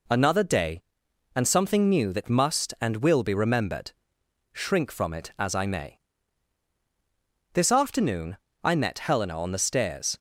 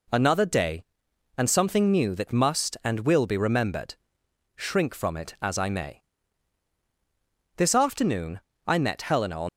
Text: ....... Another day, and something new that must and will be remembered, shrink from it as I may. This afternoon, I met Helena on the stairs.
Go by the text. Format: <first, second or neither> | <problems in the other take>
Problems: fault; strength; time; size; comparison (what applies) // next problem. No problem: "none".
first | stops before "the stairs"; at 9.4 s